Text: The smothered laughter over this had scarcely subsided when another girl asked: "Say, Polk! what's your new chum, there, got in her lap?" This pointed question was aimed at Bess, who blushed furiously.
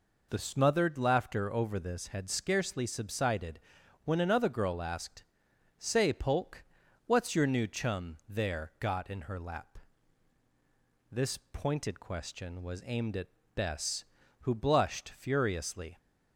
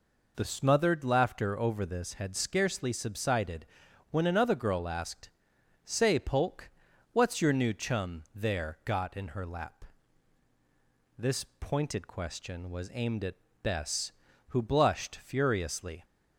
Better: neither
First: pauses between "subsided" and "when"; at 3.5 s; 0.44 s long // pauses between "at" and "Bess"; slight; at 13.2 s; 0.26 s long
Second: pauses between "subsided" and "when"; at 3.6 s; 0.44 s long // pauses between "at" and "Bess"; slight; at 13.3 s; 0.26 s long

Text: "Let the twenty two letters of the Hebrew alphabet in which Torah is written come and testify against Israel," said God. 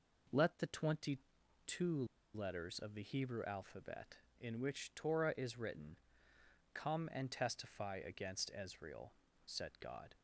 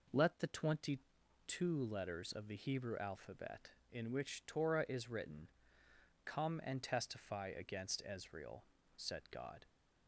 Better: second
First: pauses between "twenty" and "two"; noticeable; at 1.1 s; 0.46 s long // pauses between "two" and "letters"; slight; at 2.0 s; 0.30 s long // pauses between "written" and "come"; noticeable; at 5.9 s; 0.76 s long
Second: pauses between "twenty" and "two"; noticeable; at 1.0 s; 0.46 s long // pauses between "written" and "come"; noticeable; at 5.4 s; 0.76 s long

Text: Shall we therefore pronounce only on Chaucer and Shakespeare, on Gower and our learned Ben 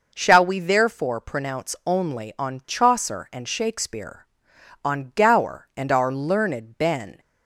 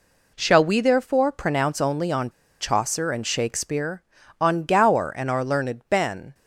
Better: first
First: none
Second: pauses between "on" and "Chaucer"; slight; at 2.3 s; 0.29 s long

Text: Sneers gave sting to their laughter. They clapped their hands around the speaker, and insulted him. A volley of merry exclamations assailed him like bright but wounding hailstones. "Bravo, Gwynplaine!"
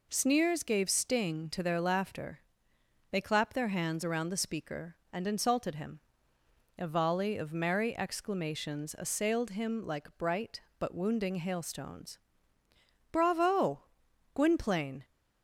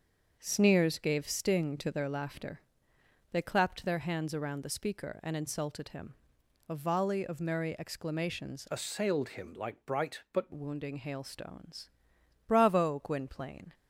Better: first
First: none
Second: starts louder than the rest; until 1.4 s; 6.5 dB // changes voice from "assailed" to "but"; from 8.6 to 10.5 s; 1.9 s long

